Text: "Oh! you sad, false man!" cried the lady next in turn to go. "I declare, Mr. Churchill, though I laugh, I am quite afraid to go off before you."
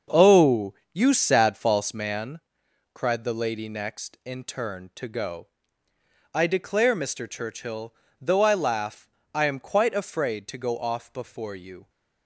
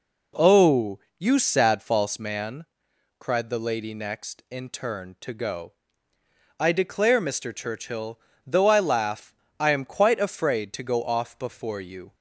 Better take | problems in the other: second | gets quieter; strong; throughout; 9.5 dB

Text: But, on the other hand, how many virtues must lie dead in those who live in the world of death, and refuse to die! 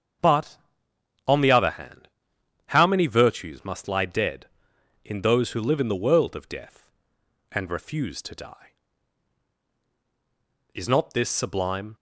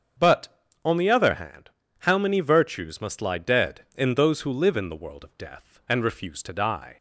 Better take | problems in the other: second | starts louder than the rest; strong; until 1.9 s; 7.5 dB; also in the second // goes on to say "Is not this sublime"; noticeable; from 10.7 s on; 1.2 s long

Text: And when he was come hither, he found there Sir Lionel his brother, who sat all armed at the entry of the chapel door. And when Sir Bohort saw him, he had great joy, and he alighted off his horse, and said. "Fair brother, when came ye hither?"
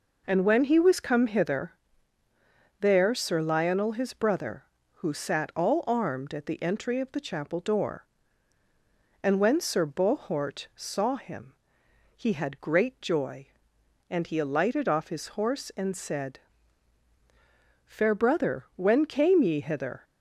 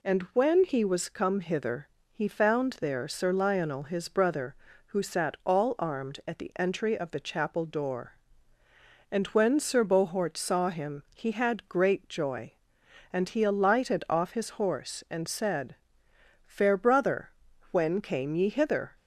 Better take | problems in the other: second | skips "he found"; at 2.2 s

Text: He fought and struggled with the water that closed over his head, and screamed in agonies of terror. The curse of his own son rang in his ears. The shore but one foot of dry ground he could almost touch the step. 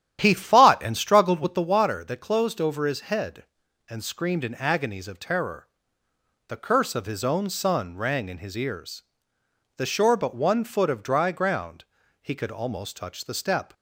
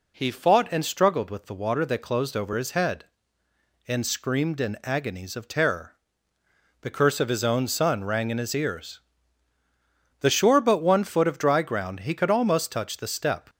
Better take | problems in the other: second | starts louder than the rest; strong; until 1.6 s; 10.5 dB // pauses between "ground" and "he"; slight; at 11.8 s; 0.36 s long

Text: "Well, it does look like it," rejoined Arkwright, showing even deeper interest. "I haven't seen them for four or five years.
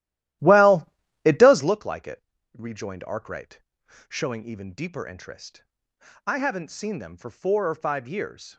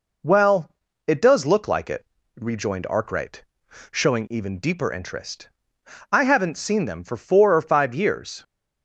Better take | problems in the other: second | starts louder than the rest; strong; until 1.8 s; 14 dB

